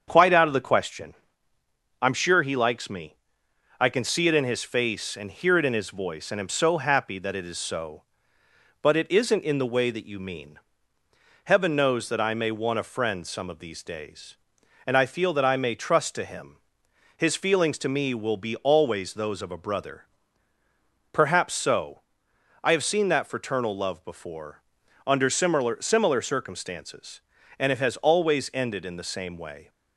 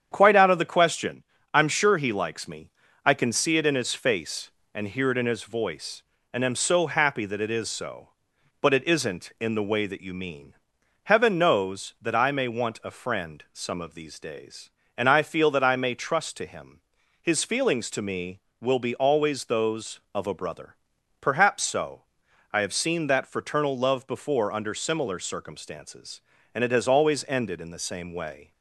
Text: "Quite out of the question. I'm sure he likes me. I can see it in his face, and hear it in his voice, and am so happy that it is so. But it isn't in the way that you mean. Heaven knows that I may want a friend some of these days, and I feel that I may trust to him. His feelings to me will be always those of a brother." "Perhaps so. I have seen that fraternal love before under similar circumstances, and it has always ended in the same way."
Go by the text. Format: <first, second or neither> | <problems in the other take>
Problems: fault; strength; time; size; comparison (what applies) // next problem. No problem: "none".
second | starts louder than the rest; strong; until 1.0 s; 7 dB; strong in the second // pauses between "before" and "under"; at 24.6 s; 0.42 s long // says "similar" twice; at 25.8 s